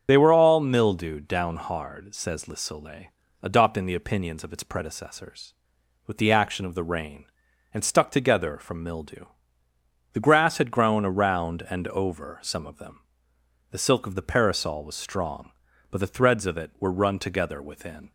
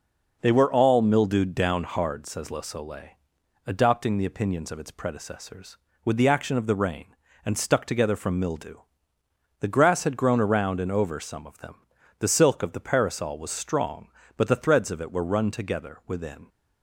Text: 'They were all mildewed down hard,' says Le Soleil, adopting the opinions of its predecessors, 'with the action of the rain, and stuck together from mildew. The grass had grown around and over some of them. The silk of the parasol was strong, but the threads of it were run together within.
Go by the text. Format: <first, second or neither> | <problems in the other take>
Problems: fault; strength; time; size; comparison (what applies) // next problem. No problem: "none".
second | loses the start of "They"; at 0.0 s; 40 ms // starts louder than the rest; noticeable; until 1.0 s; 6 dB